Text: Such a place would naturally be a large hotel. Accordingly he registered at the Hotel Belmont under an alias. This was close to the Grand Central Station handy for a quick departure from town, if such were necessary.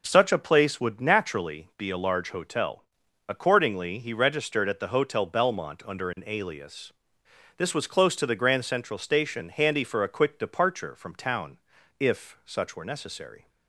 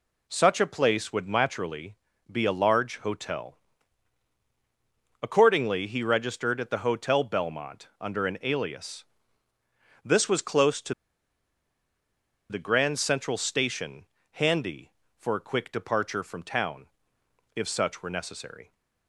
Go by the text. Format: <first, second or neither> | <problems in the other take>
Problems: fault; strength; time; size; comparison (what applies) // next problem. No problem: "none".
first | pauses between "naturally" and "be"; slight; at 1.9 s; 0.34 s long // pauses between "to" and "the"; strong; at 10.9 s; 1.5 s long // pauses between "Station" and "handy"; slight; at 14.0 s; 0.26 s long